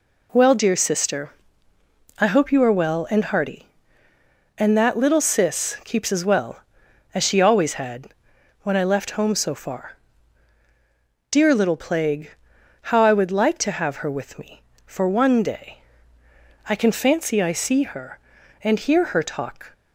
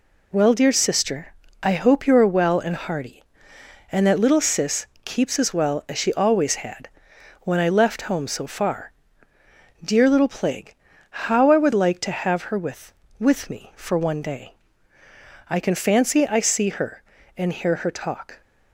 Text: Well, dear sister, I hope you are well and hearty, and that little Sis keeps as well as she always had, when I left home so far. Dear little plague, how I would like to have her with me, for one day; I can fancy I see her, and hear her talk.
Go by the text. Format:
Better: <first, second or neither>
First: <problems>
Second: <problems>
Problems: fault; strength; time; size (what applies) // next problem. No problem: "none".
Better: first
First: none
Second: pauses between "Sis" and "keeps"; slight; at 4.8 s; 0.20 s long // says "with" twice; at 13.2 s